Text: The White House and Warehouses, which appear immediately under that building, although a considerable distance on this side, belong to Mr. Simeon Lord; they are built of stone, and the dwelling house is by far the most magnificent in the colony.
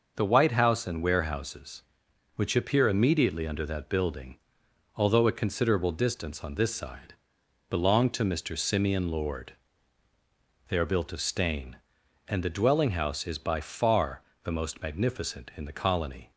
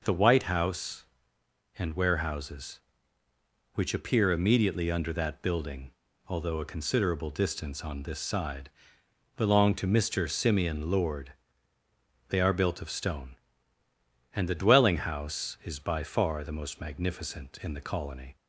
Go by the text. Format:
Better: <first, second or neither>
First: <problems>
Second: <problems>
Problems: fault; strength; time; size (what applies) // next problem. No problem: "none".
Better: second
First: says "stain" for "stone"; at 11.2 s // pauses between "far" and "the"; slight; at 14.2 s; 0.18 s long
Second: none